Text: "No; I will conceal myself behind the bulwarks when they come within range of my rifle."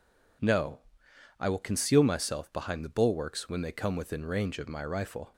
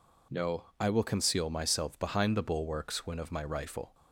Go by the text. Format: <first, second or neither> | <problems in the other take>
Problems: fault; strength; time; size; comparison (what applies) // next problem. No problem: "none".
first | skips "they come within range"; at 3.1 s